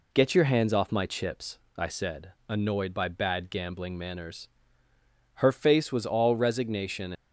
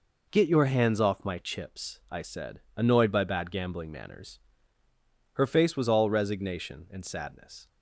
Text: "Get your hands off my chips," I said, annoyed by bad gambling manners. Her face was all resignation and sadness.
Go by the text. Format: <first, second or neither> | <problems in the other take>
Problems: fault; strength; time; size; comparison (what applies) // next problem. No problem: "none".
second | stops before "and sadness"; at 7.1 s